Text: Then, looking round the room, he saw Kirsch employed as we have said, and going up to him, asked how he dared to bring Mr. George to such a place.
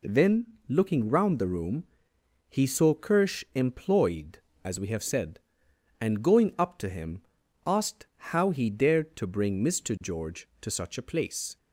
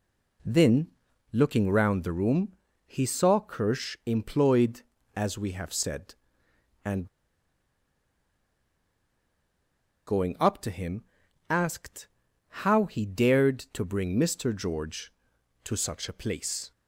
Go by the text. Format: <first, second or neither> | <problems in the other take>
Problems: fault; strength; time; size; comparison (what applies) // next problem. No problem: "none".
first | pauses between "and" and "going"; strong; at 7.0 s; 3.0 s long // pauses between "asked" and "how"; noticeable; at 12.0 s; 0.56 s long; slight in the first